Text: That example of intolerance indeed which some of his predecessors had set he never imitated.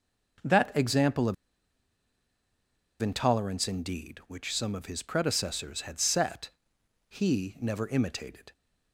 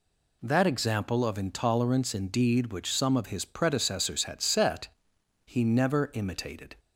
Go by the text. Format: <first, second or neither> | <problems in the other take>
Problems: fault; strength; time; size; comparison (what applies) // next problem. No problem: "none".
second | pauses between "of" and "intolerance"; strong; at 1.3 s; 1.6 s long // pauses between "set" and "he"; noticeable; at 6.4 s; 0.58 s long; noticeable in the second